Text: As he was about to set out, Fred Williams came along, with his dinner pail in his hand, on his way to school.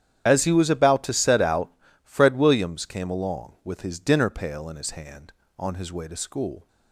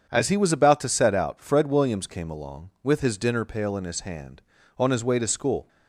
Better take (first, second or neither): second